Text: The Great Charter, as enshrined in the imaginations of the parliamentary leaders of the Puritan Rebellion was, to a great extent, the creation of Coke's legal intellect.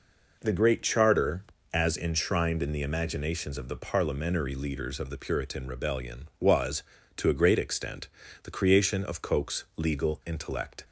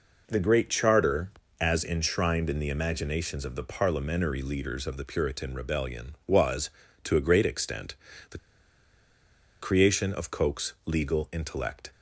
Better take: first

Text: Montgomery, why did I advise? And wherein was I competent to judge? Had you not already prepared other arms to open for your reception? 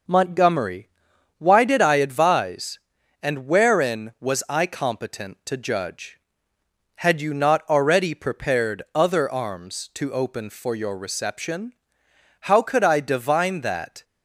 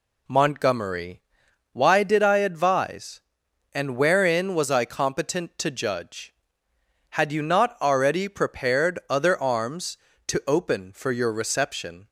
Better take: second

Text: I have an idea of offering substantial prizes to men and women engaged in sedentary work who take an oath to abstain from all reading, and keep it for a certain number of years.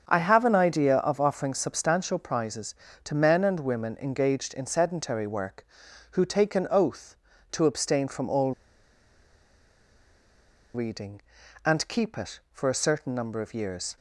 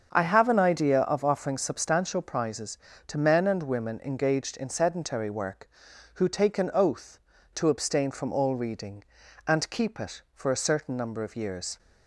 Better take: second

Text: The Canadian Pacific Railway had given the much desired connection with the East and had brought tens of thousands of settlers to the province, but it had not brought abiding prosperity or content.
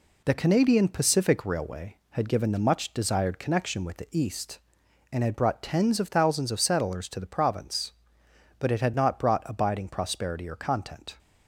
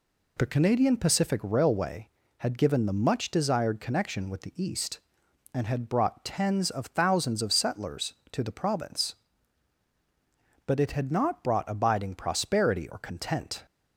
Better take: second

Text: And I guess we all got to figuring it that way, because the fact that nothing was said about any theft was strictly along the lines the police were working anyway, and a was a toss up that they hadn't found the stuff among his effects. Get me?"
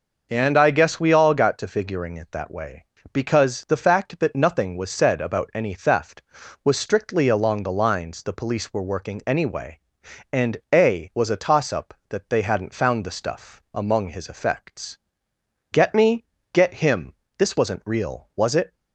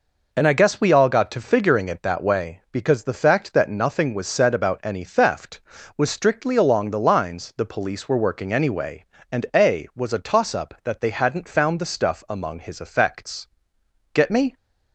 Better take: second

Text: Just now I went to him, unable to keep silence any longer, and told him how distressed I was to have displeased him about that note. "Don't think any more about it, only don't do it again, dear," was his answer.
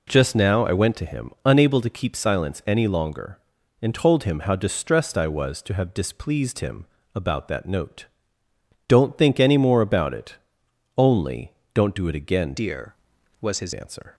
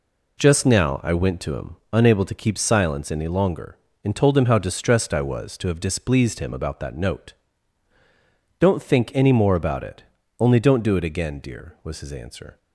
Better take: second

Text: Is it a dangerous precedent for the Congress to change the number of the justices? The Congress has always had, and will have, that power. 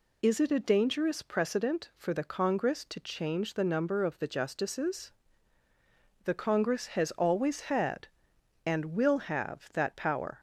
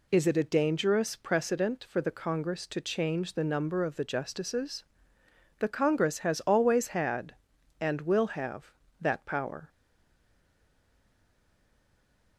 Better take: first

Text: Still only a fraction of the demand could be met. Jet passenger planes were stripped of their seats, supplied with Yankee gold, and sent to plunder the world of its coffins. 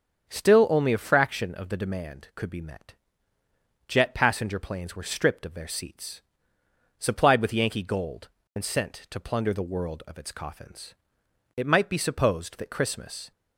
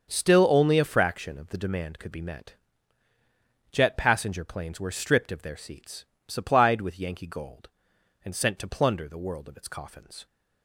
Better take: second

